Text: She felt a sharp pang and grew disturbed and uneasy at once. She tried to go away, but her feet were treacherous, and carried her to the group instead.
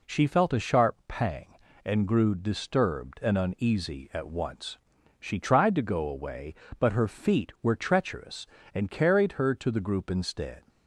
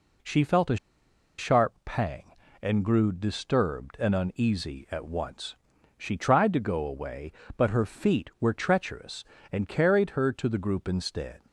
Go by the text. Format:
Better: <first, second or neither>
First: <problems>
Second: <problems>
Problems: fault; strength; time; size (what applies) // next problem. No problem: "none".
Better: first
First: none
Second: pauses between "a" and "sharp"; noticeable; at 0.7 s; 0.62 s long